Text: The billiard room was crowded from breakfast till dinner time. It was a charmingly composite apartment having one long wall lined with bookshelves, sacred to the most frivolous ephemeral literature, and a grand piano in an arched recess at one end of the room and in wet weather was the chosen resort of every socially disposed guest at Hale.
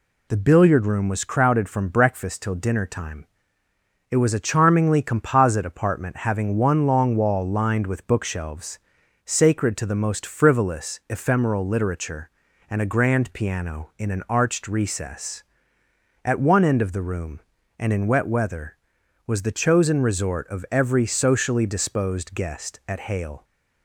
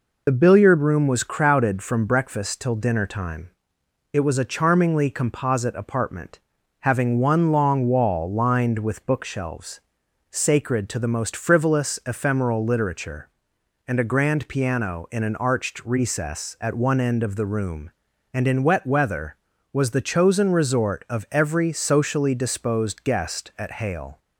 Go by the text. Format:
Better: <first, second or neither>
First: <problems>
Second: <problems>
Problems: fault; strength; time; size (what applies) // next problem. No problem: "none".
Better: first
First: none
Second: loses the start of "The"; at 0.2 s; 45 ms // pauses between "apartment" and "having"; at 6.4 s; 0.40 s long